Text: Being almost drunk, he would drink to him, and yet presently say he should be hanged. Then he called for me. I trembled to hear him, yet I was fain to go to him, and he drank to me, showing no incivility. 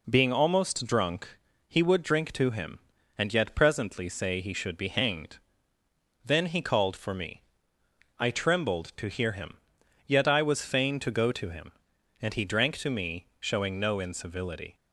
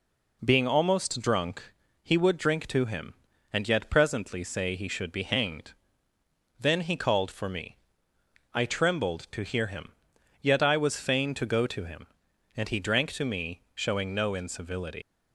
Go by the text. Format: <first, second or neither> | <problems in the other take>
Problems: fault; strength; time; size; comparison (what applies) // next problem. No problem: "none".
first | leaves "incivility" unfinished; at 15.0 s; 90 ms